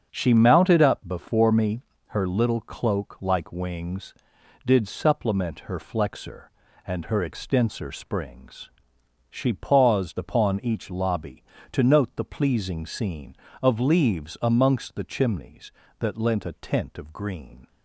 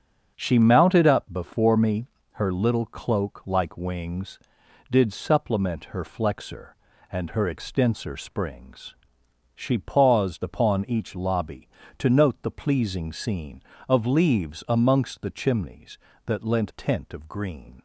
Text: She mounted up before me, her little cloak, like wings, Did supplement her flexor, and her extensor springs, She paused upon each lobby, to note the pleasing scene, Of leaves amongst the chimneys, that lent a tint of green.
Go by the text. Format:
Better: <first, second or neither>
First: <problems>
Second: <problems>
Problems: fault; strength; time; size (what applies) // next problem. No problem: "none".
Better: first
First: starts louder than the rest; until 1.1 s; 7 dB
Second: starts louder than the rest; until 1.3 s; 7 dB // skips "a"; at 16.7 s